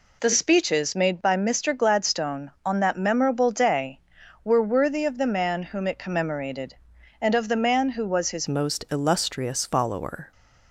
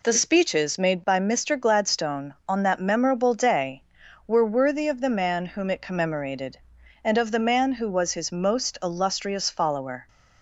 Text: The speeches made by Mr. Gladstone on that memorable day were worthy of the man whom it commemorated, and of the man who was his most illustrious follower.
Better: second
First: changes voice at "most"; from 8.4 s on; 1.9 s long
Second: none

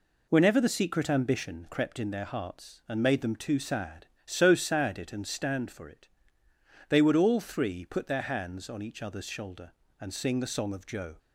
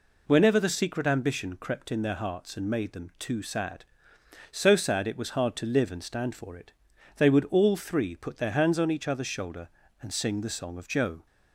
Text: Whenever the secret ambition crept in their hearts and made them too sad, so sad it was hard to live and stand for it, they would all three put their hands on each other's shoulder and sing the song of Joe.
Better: second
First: skips "was hard to live"; at 5.1 s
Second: none

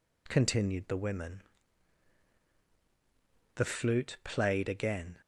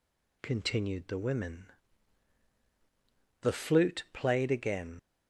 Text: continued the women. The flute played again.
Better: first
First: none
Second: leaves "again" unfinished; at 4.9 s; 55 ms

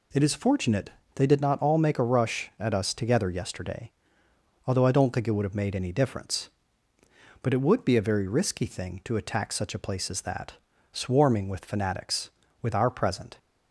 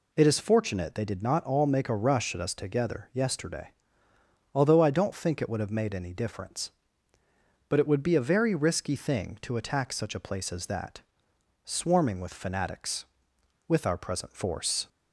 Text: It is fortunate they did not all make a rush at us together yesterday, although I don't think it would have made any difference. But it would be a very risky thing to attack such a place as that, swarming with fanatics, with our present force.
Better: second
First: pauses between "fortunate" and "they"; slight; at 0.8 s; 0.24 s long // stops before "force"; at 13.3 s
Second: none

